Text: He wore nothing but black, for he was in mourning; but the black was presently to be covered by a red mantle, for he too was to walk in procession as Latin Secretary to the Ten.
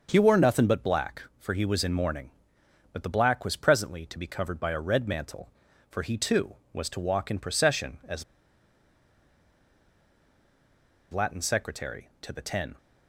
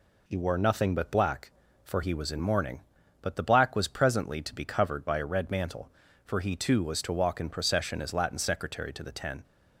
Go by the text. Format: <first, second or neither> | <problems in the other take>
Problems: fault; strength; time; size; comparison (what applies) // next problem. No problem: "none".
second | starts louder than the rest; until 1.1 s; 6.5 dB // pauses between "as" and "Latin"; strong; at 8.2 s; 2.8 s long